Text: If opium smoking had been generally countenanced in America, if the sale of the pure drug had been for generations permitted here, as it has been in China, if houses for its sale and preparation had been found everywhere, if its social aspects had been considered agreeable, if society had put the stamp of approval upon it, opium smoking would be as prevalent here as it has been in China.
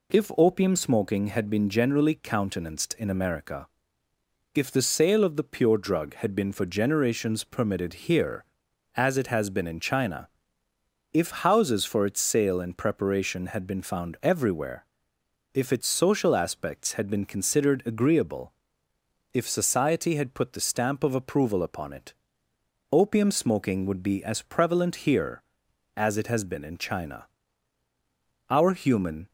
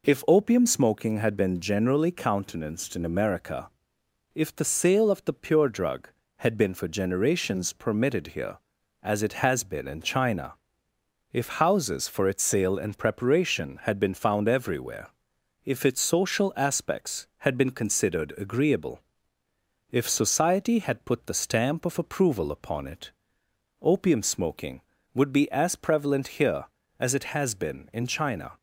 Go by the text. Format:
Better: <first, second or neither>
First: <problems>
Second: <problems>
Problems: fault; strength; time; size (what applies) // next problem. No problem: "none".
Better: second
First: goes on to say "Our human"; noticeable; from 28.4 s on; 0.82 s long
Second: none